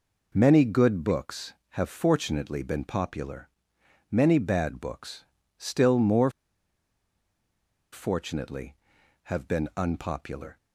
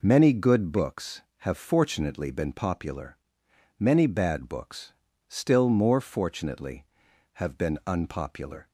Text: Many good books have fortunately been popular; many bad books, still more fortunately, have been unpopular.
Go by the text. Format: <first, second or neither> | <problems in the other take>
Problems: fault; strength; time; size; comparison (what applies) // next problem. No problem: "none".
second | pauses between "more" and "fortunately"; strong; at 6.3 s; 1.6 s long